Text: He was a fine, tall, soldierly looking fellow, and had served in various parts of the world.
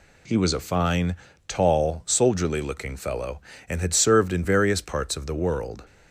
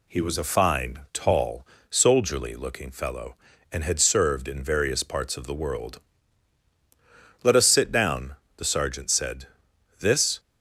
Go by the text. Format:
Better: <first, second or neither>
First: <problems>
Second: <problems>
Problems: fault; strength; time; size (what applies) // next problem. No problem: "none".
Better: first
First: none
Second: goes on to say "Let us sit down the sergeant said this"; strong; from 7.4 s on; 2.9 s long